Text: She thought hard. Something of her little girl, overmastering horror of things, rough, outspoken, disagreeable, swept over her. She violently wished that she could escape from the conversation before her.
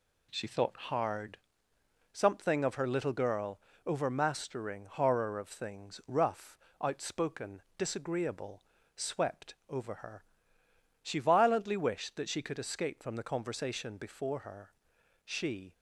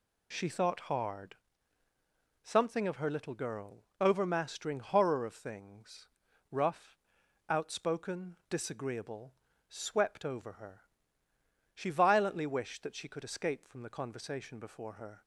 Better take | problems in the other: second | goes on to say "She"; slight; from 15.2 s on; 0.48 s long

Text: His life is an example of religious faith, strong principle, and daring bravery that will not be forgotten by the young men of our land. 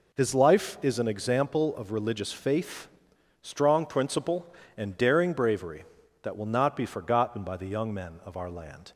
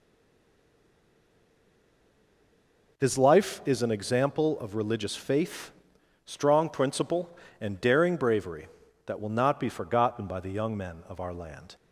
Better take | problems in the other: first | stays silent before the first word; strong; until 2.9 s; 2.9 s long

